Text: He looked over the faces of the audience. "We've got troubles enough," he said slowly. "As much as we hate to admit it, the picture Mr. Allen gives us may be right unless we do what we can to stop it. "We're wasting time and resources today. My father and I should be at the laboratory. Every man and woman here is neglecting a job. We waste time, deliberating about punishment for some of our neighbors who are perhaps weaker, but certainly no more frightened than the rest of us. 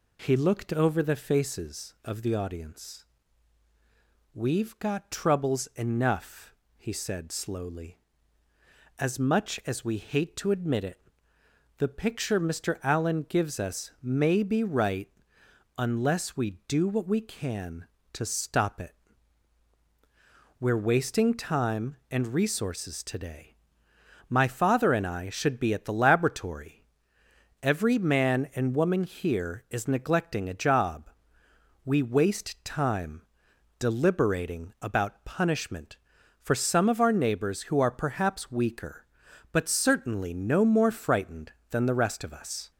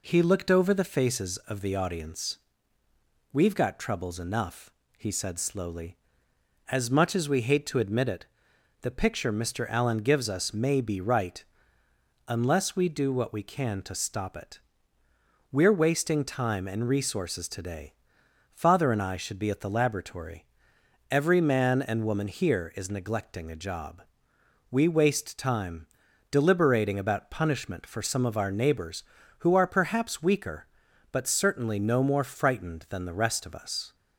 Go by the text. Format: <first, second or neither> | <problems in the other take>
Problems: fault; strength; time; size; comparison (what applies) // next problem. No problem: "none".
first | pauses between "right" and "unless"; noticeable; at 11.4 s; 0.84 s long; noticeable in the first // skips "My"; at 18.2 s